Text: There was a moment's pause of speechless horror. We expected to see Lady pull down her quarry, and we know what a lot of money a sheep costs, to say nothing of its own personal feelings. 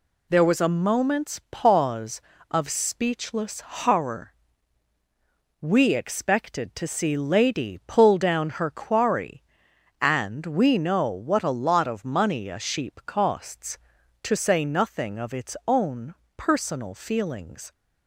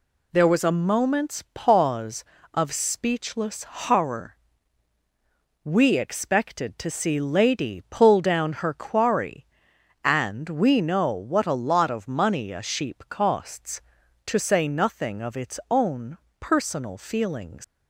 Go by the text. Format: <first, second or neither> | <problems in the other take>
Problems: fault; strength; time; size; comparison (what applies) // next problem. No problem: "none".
first | pauses between "own" and "personal"; slight; at 16.1 s; 0.22 s long; slight in the first // leaves "feelings" unfinished; at 17.6 s; 100 ms